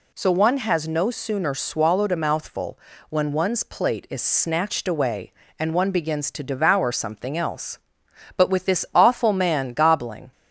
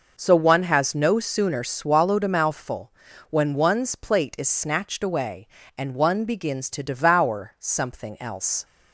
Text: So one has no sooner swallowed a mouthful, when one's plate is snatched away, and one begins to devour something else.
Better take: second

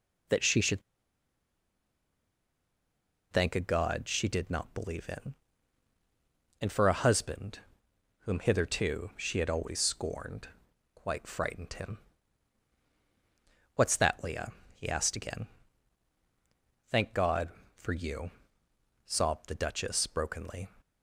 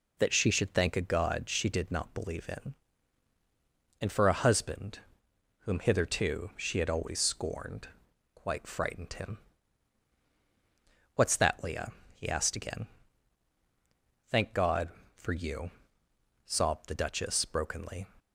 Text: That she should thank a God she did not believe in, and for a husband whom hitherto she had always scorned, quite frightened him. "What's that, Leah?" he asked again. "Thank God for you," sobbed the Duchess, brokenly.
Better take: second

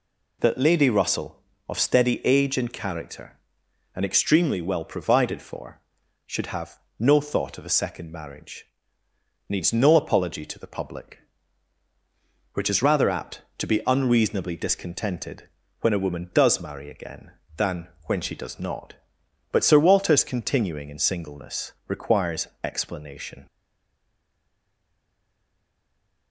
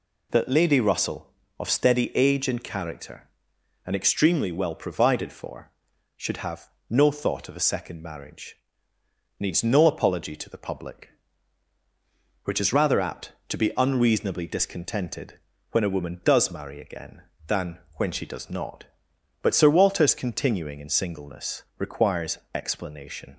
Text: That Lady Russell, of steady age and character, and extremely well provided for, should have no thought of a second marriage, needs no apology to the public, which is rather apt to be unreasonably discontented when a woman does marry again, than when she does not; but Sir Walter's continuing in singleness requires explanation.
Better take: second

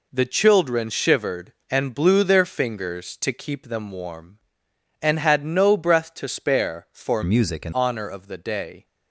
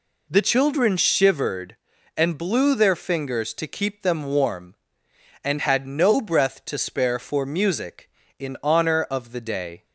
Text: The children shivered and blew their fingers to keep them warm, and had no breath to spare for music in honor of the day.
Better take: second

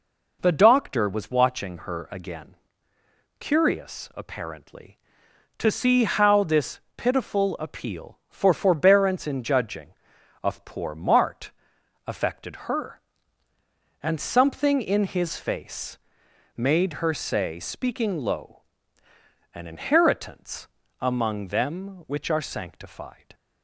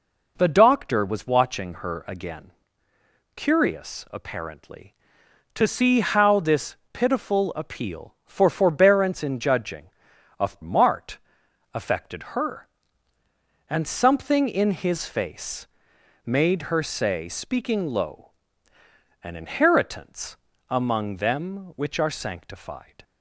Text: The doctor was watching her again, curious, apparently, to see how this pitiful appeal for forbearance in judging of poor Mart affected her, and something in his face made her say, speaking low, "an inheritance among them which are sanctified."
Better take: first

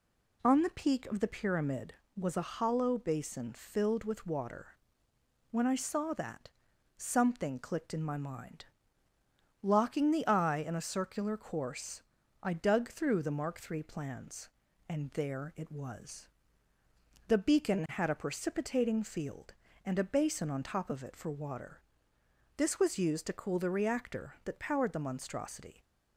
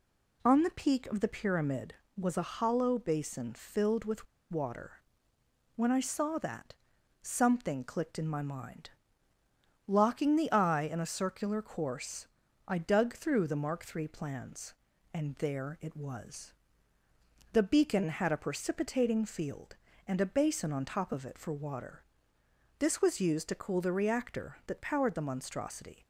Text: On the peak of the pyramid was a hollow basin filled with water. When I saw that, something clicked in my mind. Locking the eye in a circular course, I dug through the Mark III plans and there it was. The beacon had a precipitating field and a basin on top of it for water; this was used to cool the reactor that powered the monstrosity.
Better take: first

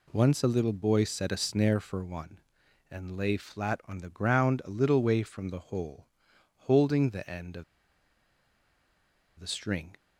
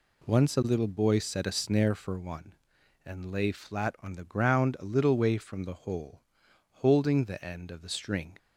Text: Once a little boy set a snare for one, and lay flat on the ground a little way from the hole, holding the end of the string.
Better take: second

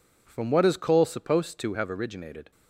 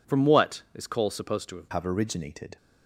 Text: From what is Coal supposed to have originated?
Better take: first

